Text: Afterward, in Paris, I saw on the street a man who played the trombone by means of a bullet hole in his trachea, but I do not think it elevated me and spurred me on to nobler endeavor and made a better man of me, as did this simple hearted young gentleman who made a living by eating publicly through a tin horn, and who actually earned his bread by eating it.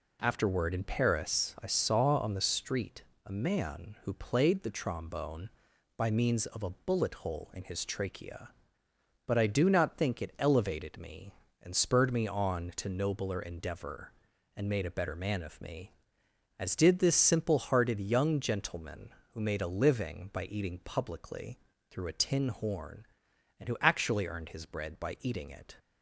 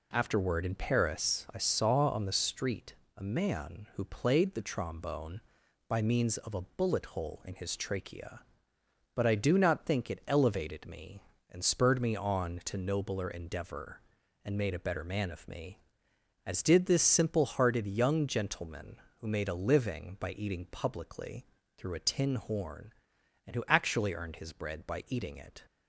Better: neither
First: pauses between "street" and "a"; slight; at 3.0 s; 0.22 s long // pauses between "publicly" and "through"; slight; at 21.5 s; 0.32 s long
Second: pauses between "street" and "a"; slight; at 2.9 s; 0.22 s long // pauses between "publicly" and "through"; slight; at 21.4 s; 0.32 s long

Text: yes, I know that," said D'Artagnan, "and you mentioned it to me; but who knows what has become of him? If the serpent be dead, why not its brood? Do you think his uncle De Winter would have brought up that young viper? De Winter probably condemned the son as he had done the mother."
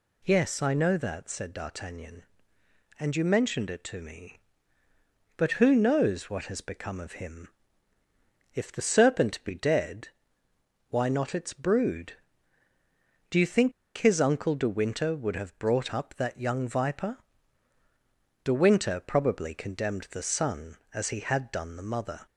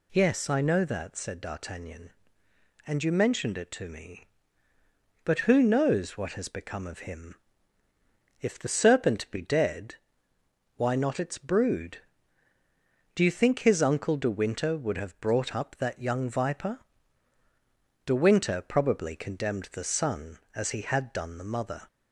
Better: second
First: pauses between "think" and "his"; slight; at 13.7 s; 0.25 s long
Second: none

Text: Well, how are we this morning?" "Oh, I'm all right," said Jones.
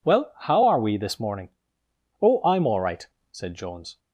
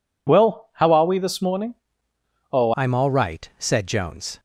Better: first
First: none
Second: changes voice at "I'm"; from 2.7 s on; 1.6 s long

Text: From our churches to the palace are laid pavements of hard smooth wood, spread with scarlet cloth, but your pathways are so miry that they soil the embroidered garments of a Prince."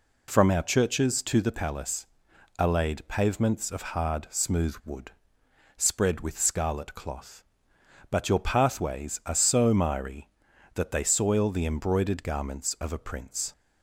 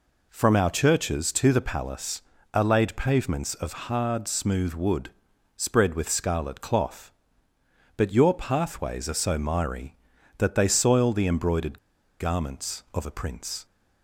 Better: first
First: none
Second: pauses between "embroidered" and "garments"; at 11.7 s; 0.44 s long

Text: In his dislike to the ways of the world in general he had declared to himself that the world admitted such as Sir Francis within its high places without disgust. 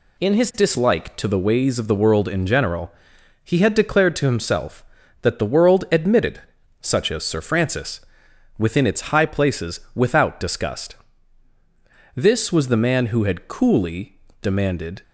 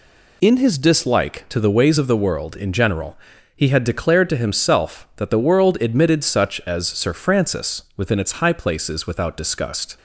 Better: second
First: pauses between "general" and "he"; noticeable; at 2.9 s; 0.52 s long // pauses between "admitted" and "such"; at 6.4 s; 0.40 s long // pauses between "Francis" and "within"; noticeable; at 8.0 s; 0.56 s long // pauses between "places" and "without"; slight; at 9.7 s; 0.16 s long // goes on to say "This was the man who had coolly demanded"; strong; from 12.1 s on; 2.8 s long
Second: pauses between "general" and "he"; at 3.1 s; 0.38 s long

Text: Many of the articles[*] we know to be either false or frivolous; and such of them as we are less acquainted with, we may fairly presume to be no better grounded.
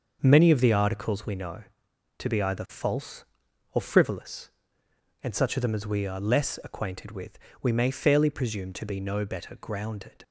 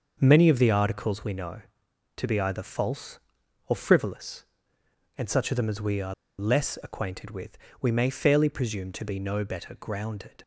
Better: first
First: starts louder than the rest; until 1.2 s; 6.5 dB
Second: starts louder than the rest; until 1.2 s; 6.5 dB // pauses between "are" and "less"; slight; at 6.1 s; 0.26 s long

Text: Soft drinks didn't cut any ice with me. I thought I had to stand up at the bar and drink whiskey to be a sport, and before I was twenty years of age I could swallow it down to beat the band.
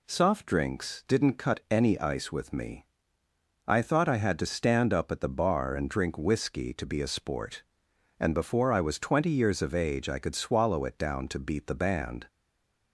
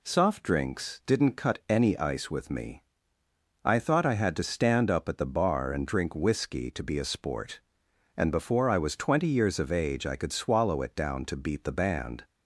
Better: second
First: stays silent after the last word; slight; from 12.2 s on; 0.7 s long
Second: none

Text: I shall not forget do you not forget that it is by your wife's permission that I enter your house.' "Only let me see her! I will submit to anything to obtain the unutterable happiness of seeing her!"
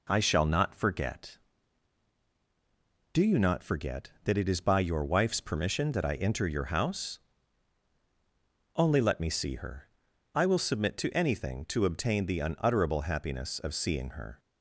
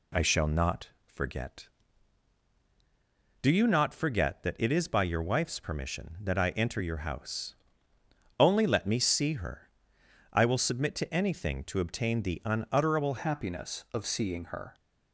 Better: first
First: none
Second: pauses between "not" and "forget"; slight; at 0.8 s; 0.16 s long // changes voice at "happiness"; from 13.1 s on; 1.6 s long

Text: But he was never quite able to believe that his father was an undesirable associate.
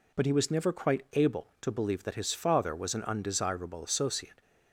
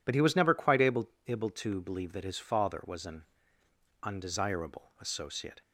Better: first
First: none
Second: says "able" twice; at 1.2 s // pauses between "an" and "undesirable"; noticeable; at 3.2 s; 0.78 s long

